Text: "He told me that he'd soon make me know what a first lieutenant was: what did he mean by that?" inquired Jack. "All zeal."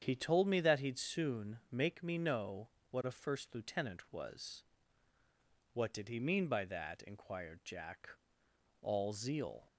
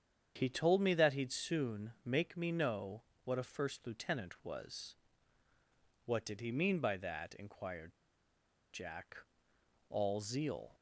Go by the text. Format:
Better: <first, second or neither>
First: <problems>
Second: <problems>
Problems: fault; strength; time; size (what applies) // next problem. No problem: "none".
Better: first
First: starts louder than the rest; strong; until 1.0 s; 8 dB // pauses between "know" and "what"; slight; at 2.6 s; 0.24 s long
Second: starts louder than the rest; strong; until 1.3 s; 8 dB // pauses between "know" and "what"; slight; at 3.0 s; 0.24 s long // pauses between "inquired" and "Jack"; noticeable; at 7.9 s; 0.75 s long